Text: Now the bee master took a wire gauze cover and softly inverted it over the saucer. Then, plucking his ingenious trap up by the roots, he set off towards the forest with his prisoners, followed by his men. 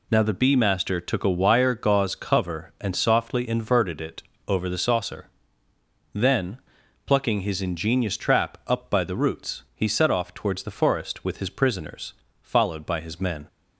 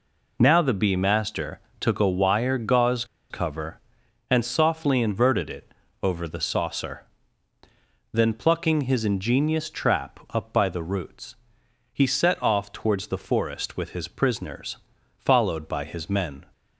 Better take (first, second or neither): first